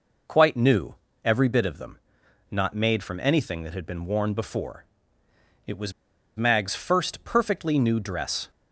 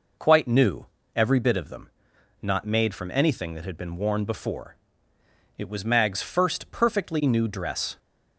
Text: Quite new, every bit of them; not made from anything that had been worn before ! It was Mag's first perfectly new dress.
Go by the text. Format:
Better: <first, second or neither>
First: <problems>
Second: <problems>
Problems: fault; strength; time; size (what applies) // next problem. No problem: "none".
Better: second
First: pauses between "was" and "Mag's"; at 5.9 s; 0.45 s long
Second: none